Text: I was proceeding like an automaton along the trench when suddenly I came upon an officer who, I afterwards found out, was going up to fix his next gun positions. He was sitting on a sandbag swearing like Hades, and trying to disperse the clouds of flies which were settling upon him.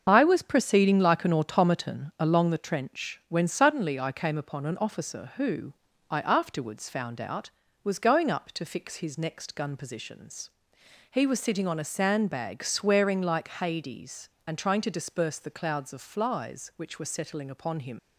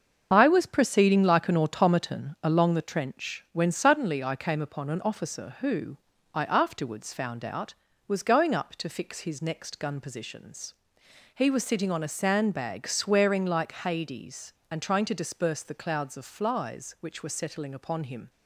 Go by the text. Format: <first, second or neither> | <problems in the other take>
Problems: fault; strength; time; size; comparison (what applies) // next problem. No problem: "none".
second | starts louder than the rest; until 1.0 s; 6.5 dB; also in the second // leaves "him" unfinished; at 17.9 s; 70 ms